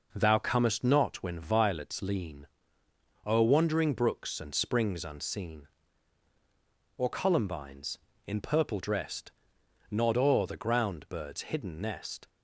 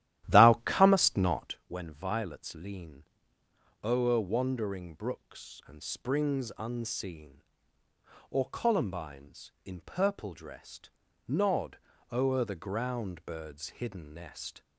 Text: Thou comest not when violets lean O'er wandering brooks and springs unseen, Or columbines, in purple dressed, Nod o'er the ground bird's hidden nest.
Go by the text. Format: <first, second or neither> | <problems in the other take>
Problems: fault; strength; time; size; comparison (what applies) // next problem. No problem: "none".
first | starts louder than the rest; strong; until 1.6 s; 13 dB // pauses between "lean" and "O'er"; noticeable; at 3.0 s; 0.80 s long; noticeable in the first // pauses between "Nod" and "o'er"; slight; at 11.7 s; 0.34 s long